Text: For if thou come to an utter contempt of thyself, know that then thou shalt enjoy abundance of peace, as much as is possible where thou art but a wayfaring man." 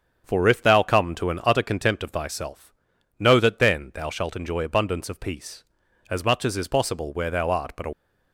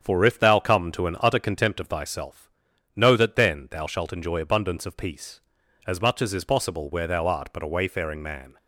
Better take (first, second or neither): second